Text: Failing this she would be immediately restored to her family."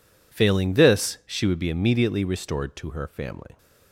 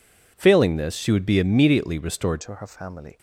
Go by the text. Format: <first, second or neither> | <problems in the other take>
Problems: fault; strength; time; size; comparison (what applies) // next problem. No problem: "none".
first | changes voice at "to"; from 2.4 s on; 0.7 s long